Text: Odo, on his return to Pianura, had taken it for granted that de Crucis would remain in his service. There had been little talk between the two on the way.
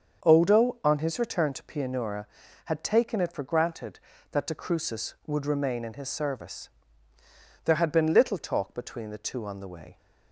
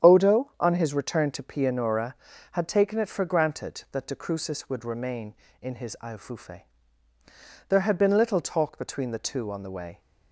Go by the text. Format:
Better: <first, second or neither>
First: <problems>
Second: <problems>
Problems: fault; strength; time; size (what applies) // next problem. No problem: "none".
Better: first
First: starts louder than the rest; until 1.2 s; 7 dB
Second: starts louder than the rest; strong; until 1.1 s; 9 dB // says "iofufe" for "service"; at 6.0 s